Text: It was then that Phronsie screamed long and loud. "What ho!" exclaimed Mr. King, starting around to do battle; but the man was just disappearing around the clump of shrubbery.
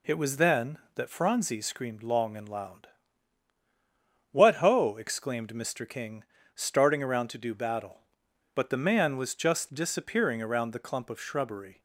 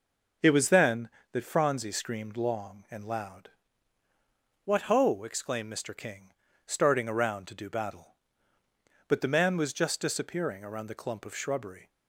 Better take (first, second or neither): neither